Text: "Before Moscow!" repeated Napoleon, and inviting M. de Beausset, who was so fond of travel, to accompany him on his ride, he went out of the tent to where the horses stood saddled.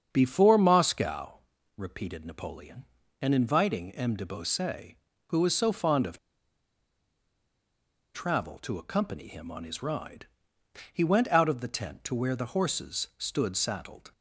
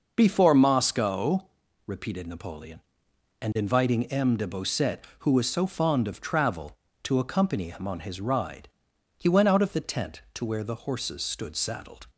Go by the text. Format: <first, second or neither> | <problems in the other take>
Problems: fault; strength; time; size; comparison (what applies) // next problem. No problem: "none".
second | starts louder than the rest; strong; until 1.1 s; 7 dB // pauses between "of" and "travel"; strong; at 6.1 s; 1.9 s long